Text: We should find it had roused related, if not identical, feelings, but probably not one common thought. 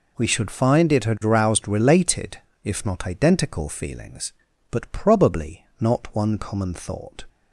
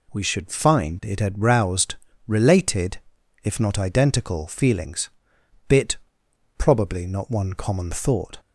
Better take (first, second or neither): first